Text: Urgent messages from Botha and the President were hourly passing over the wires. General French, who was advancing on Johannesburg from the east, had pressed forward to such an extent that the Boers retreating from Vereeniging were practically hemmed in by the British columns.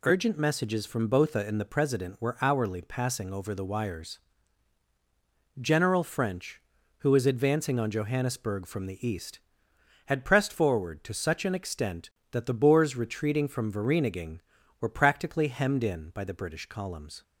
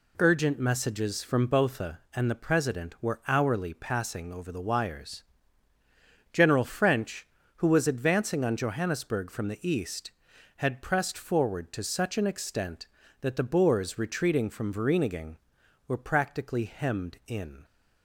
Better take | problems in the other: first | stops before "by the British columns"; at 17.6 s

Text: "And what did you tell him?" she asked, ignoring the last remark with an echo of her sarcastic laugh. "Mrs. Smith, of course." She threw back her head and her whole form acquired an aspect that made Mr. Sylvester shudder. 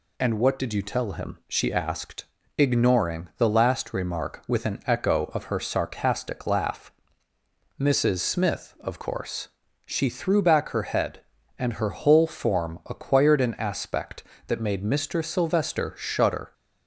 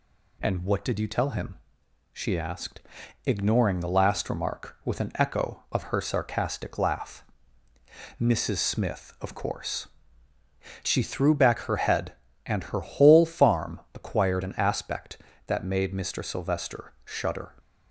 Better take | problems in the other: first | says "farm" for "form"; at 13.2 s

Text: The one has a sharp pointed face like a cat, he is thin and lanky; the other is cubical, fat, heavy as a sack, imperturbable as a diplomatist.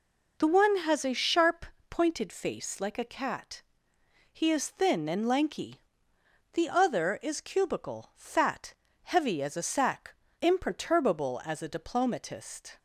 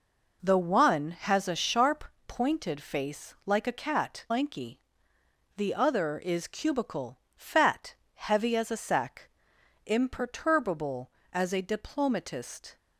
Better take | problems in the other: first | pauses between "sharp" and "pointed"; slight; at 2.0 s; 0.24 s long; slight in the first // skips "he is thin and"; at 4.2 s

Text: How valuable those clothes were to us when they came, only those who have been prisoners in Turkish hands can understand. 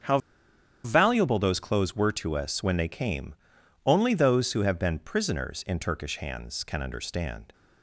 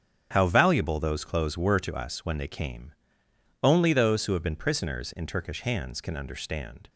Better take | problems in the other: second | starts louder than the rest; strong; until 1.7 s; 7 dB; strong in the second // pauses between "How" and "valuable"; noticeable; at 0.1 s; 0.66 s long

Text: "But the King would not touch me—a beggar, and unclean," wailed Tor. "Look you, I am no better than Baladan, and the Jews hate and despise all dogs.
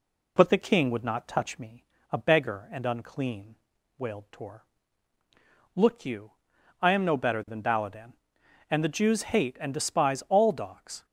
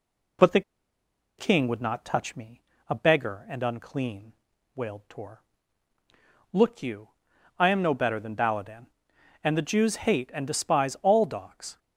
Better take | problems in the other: first | pauses between "the" and "King"; noticeable; at 0.6 s; 0.76 s long

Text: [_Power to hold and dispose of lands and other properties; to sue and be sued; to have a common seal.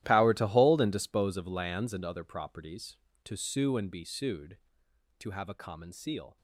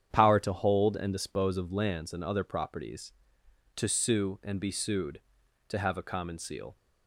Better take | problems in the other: second | gets quieter; strong; throughout; 17 dB // starts louder than the rest; strong; until 1.0 s; 13.5 dB; strong in the second

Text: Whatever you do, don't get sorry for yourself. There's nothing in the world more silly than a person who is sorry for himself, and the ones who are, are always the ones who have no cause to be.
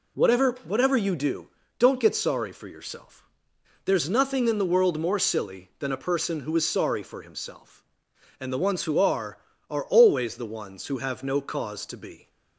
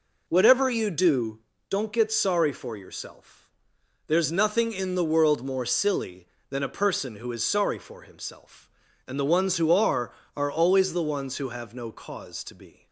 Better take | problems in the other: second | says "Whatever" twice; at 0.6 s

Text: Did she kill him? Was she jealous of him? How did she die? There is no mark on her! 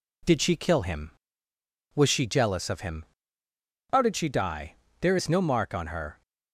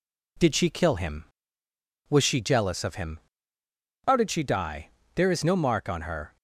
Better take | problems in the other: neither | none

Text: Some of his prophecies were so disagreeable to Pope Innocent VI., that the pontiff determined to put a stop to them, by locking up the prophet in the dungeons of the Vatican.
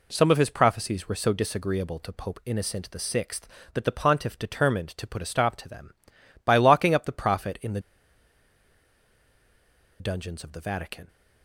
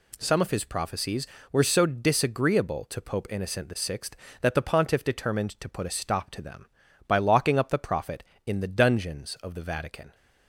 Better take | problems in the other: second | pauses between "the" and "dungeons"; strong; at 7.7 s; 2.2 s long

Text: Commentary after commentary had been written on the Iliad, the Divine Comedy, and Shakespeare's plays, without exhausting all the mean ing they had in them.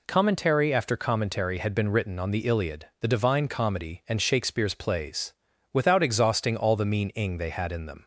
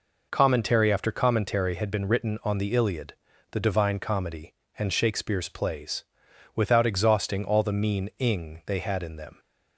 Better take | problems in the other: neither | none

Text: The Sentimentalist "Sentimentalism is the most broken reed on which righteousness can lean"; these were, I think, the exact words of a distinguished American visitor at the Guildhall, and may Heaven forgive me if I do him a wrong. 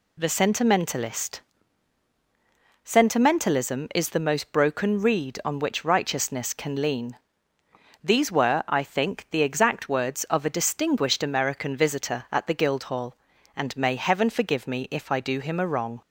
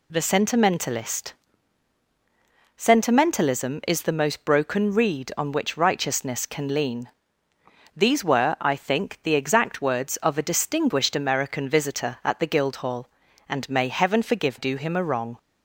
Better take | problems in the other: first | pauses between "Sentimentalist" and "Sentimentalism"; strong; at 1.3 s; 1.4 s long; strong in the first // skips "me if I"; at 14.5 s

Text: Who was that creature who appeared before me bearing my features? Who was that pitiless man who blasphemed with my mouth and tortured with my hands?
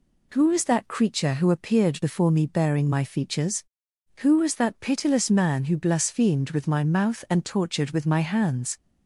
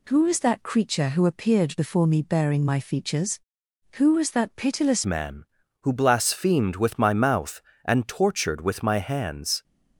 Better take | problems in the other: first | changes voice at "man"; from 5.0 s on; 4.6 s long

